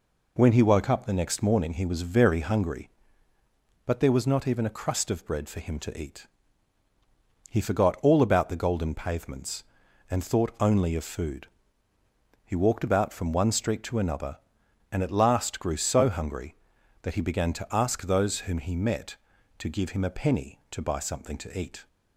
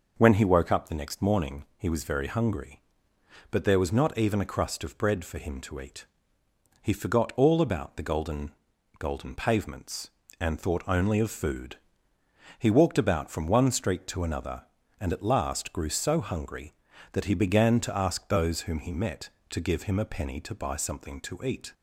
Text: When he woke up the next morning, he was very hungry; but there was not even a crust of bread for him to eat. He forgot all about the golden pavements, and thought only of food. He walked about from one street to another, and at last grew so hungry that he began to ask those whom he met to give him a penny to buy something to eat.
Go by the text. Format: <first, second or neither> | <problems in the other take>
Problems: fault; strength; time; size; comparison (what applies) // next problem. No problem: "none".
first | says "golden" twice; at 8.9 s